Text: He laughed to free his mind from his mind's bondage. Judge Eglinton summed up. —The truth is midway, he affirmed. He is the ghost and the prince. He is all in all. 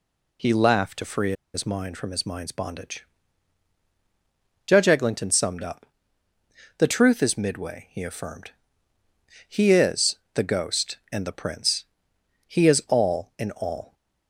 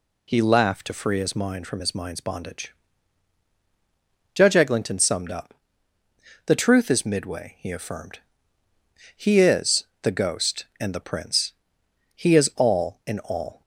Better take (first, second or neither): second